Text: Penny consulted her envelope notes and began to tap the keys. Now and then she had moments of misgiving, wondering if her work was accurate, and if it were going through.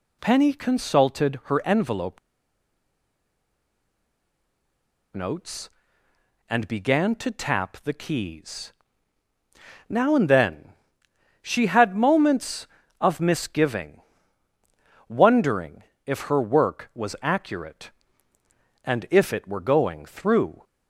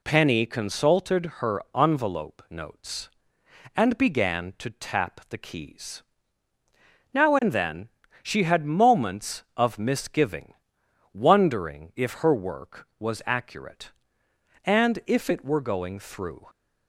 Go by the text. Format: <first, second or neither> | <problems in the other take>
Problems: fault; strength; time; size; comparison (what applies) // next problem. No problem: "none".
second | pauses between "envelope" and "notes"; strong; at 2.1 s; 2.9 s long // pauses between "then" and "she"; noticeable; at 10.6 s; 0.72 s long; slight in the second // pauses between "wondering" and "if"; slight; at 15.8 s; 0.22 s long